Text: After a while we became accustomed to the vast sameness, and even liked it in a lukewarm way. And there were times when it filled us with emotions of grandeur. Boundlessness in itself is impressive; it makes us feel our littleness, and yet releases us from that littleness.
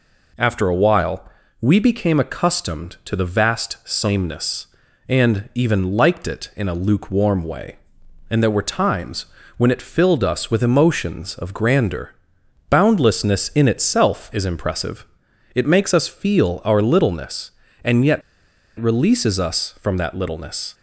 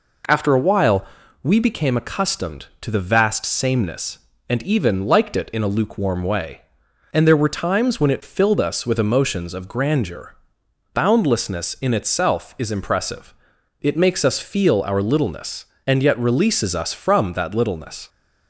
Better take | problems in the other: second | pauses between "while" and "we"; slight; at 1.2 s; 0.34 s long; also in the second // pauses between "times" and "when"; slight; at 9.2 s; 0.32 s long // pauses between "yet" and "releases"; noticeable; at 18.2 s; 0.59 s long

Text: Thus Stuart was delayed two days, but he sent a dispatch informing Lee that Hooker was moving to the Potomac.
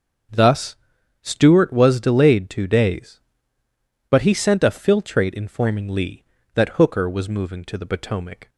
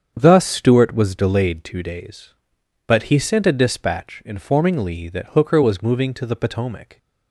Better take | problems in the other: second | starts louder than the rest; until 1.7 s; 6.5 dB; strong in the second // pauses between "Thus" and "Stuart"; noticeable; at 0.7 s; 0.46 s long // says "filtrate" for "dispatch"; at 4.7 s

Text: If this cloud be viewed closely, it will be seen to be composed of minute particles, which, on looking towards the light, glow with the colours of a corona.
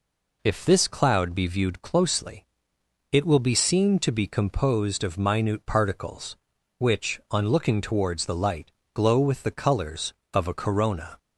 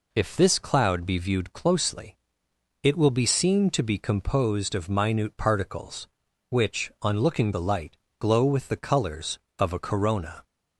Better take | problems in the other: first | skips "towards"; at 7.5 s

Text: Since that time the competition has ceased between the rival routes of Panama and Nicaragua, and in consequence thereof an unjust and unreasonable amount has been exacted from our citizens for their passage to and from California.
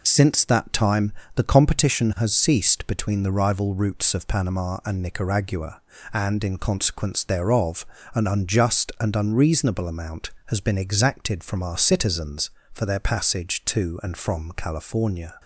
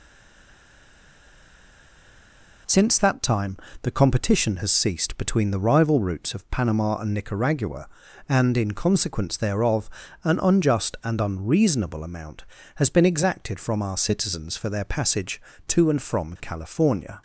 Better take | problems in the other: first | stays silent before the first word; strong; until 2.6 s; 2.6 s long // pauses between "time" and "the"; slight; at 3.5 s; 0.26 s long; slight in the first // pauses between "thereof" and "an"; slight; at 9.8 s; 0.34 s long; slight in the first

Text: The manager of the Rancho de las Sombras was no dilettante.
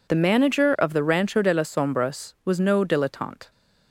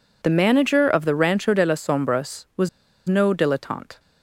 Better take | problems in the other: first | pauses between "was" and "no"; at 2.6 s; 0.40 s long

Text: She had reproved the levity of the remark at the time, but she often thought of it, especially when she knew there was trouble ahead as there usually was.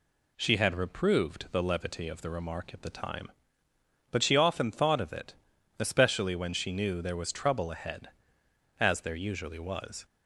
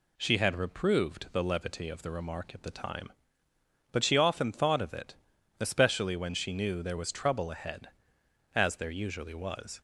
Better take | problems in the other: neither | none

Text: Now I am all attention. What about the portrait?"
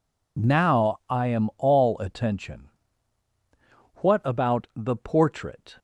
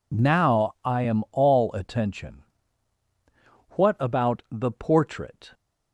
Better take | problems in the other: neither | none

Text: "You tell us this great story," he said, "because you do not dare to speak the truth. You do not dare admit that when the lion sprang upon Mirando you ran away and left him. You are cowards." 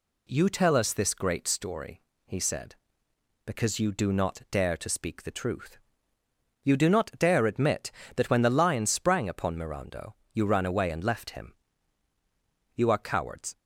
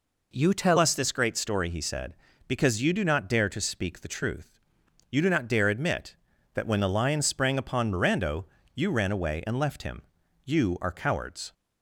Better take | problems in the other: first | changes voice at "us"; from 0.7 s on; 10.8 s long // pauses between "Mirando" and "you"; slight; at 8.4 s; 0.30 s long; slight in the first

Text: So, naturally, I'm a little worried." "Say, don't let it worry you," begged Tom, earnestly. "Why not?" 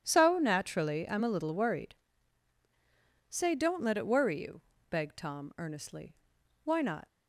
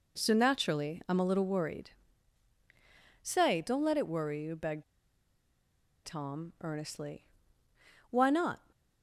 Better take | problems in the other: first | pauses between "begged" and "Tom"; at 4.8 s; 1.2 s long

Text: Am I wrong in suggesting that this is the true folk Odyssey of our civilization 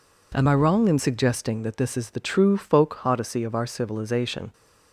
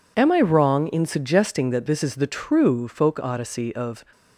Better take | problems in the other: first | stops before "our civilization"; at 4.1 s

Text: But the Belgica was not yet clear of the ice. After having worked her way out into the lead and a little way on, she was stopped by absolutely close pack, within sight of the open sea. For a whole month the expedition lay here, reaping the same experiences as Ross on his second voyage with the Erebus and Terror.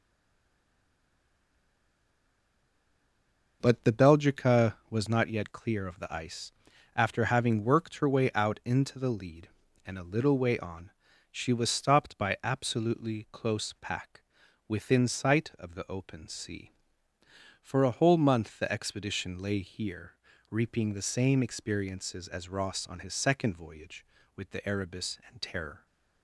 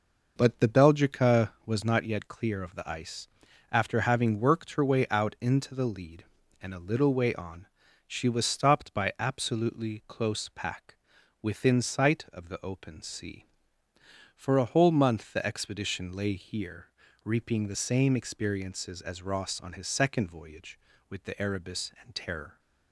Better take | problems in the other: second | stays silent before the first word; strong; until 3.6 s; 3.6 s long

